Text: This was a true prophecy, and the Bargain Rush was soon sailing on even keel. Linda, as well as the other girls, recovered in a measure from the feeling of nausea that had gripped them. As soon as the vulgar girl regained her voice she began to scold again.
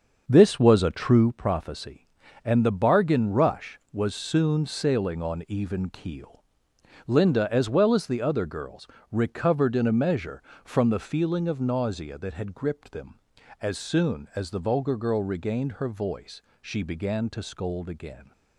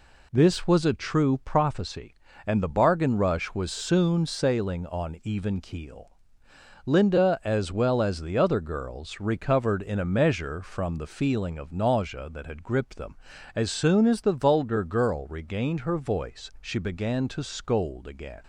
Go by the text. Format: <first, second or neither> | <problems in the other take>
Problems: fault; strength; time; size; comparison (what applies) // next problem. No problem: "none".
second | starts louder than the rest; until 1.4 s; 6.5 dB // pauses between "voice" and "she"; slight; at 16.4 s; 0.18 s long